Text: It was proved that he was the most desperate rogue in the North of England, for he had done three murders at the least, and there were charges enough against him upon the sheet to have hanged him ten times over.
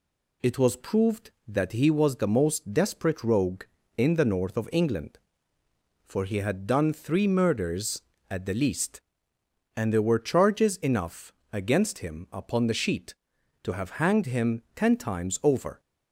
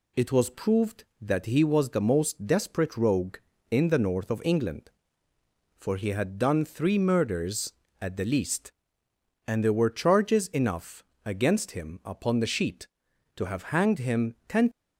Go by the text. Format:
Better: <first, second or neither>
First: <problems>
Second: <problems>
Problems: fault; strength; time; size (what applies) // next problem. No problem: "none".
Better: first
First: pauses between "enough" and "against"; slight; at 11.3 s; 0.18 s long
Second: pauses between "enough" and "against"; slight; at 11.0 s; 0.20 s long // stops before "times over"; at 14.7 s